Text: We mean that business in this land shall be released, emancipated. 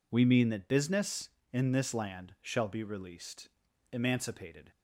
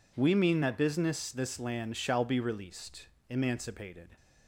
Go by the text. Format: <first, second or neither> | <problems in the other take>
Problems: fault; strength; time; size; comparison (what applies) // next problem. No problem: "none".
first | skips "in"; at 1.2 s